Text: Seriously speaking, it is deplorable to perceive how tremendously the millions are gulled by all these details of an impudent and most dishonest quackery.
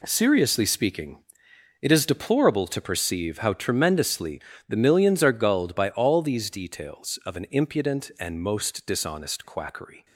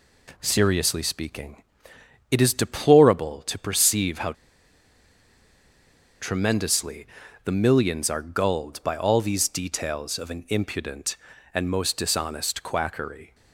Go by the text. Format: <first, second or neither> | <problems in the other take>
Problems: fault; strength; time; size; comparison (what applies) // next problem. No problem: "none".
first | pauses between "how" and "tremendously"; strong; at 4.3 s; 1.8 s long // pauses between "tremendously" and "the"; at 7.0 s; 0.38 s long; slight in the first